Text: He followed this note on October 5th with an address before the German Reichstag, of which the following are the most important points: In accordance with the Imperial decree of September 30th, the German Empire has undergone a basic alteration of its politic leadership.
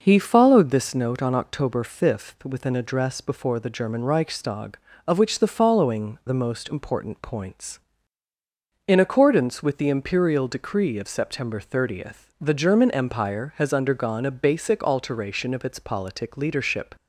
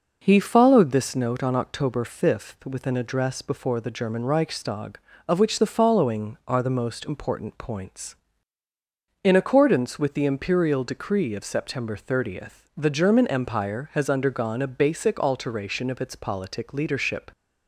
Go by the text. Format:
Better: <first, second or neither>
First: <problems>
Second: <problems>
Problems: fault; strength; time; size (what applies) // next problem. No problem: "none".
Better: second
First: skips "are"; at 6.2 s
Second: none